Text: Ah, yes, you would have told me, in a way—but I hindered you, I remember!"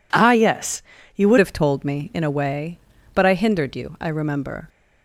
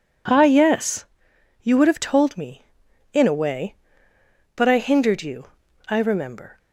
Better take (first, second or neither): second